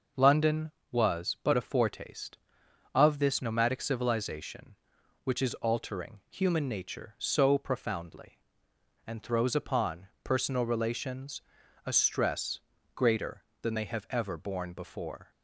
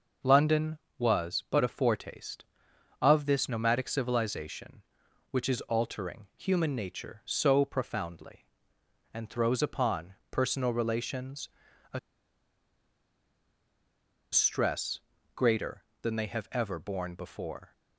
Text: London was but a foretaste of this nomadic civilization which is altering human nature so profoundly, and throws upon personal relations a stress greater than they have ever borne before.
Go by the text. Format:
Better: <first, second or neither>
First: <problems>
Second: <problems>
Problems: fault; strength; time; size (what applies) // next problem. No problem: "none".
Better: first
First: pauses between "relations" and "a"; noticeable; at 11.4 s; 0.46 s long // pauses between "stress" and "greater"; slight; at 12.6 s; 0.34 s long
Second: pauses between "relations" and "a"; noticeable; at 11.4 s; 0.46 s long // pauses between "a" and "stress"; strong; at 11.9 s; 2.3 s long // pauses between "stress" and "greater"; slight; at 15.0 s; 0.34 s long